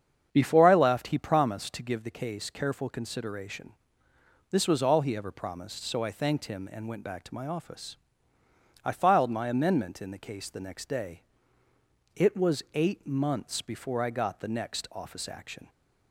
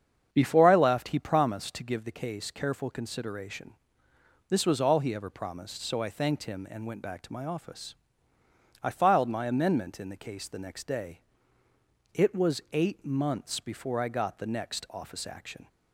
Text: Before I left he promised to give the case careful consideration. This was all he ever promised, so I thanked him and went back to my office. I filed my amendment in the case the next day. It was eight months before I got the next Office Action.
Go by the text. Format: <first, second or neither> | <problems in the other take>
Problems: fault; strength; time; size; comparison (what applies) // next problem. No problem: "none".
neither | starts louder than the rest; strong; the same in both